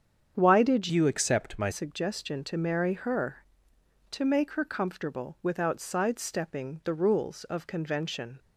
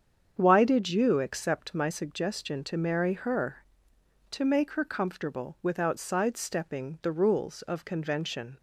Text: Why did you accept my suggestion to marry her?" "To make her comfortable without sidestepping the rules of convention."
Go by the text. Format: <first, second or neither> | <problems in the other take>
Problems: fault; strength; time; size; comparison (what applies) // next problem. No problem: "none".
second | starts louder than the rest; strong; until 1.4 s; 8 dB; strong in the second // changes voice from "you" to "my"; from 0.9 to 1.6 s; 0.7 s long